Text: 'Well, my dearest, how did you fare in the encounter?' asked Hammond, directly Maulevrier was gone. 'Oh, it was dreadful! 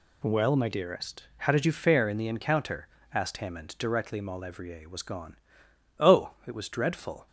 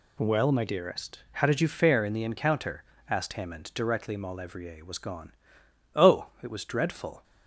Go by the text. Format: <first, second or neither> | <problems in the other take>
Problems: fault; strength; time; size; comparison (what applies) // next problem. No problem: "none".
neither | none